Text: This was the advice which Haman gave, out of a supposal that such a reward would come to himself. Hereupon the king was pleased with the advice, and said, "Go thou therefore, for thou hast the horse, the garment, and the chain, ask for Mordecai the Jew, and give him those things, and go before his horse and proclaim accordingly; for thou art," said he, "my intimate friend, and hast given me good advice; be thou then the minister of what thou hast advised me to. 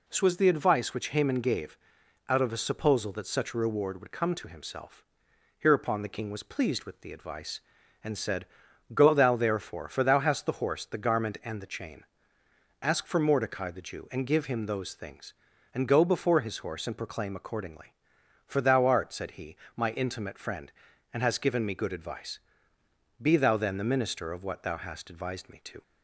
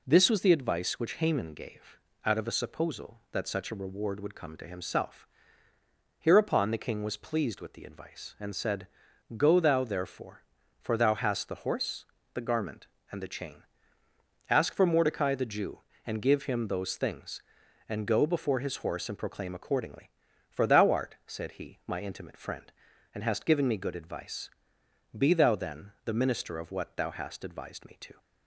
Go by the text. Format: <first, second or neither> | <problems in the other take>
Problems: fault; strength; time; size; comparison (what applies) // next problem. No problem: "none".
neither | none